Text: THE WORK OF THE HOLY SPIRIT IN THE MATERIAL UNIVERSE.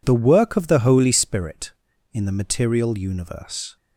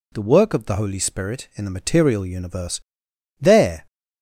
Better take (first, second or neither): first